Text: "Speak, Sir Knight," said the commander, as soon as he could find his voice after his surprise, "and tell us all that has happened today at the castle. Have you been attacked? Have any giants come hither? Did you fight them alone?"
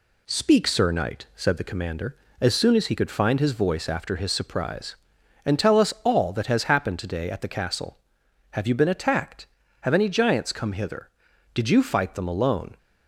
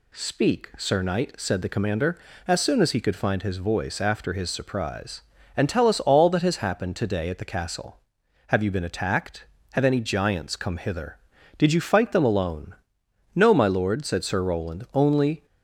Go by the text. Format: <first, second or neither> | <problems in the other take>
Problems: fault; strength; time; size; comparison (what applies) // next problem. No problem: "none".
first | goes on to say "No my Lord said Sir Roland Only"; strong; from 13.3 s on; 2.1 s long